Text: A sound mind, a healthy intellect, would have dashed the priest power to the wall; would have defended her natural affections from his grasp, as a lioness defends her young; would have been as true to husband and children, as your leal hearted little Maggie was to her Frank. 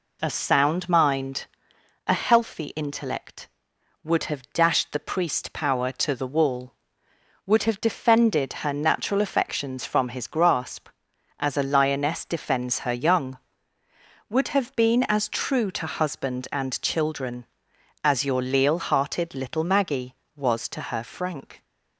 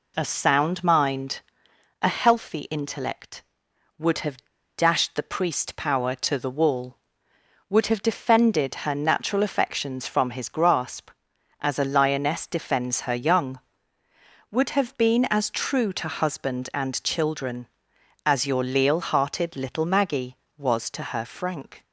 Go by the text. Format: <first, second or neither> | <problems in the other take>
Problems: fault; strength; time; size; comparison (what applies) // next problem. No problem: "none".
first | pauses between "have" and "dashed"; at 4.3 s; 0.40 s long